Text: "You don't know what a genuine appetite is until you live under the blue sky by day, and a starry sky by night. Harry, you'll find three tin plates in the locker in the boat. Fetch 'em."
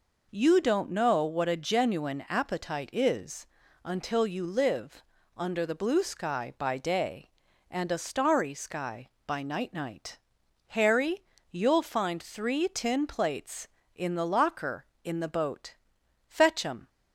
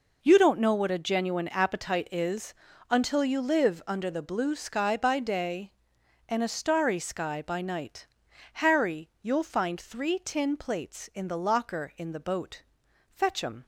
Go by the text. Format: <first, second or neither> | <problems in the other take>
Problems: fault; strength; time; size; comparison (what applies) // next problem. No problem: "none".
second | pauses between "is" and "until"; at 3.4 s; 0.38 s long; also in the second // pauses between "live" and "under"; slight; at 5.0 s; 0.34 s long // says "night" twice; at 9.7 s